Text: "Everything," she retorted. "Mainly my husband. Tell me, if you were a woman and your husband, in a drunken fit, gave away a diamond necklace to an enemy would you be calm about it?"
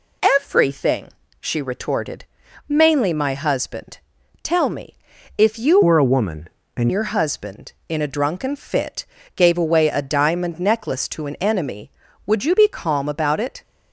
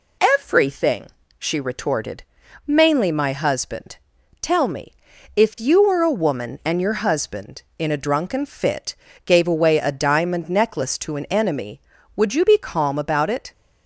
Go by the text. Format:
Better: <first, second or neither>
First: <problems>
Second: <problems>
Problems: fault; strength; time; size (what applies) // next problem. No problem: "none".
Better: second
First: changes voice from "were" to "and"; from 5.8 to 6.8 s; 1.0 s long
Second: none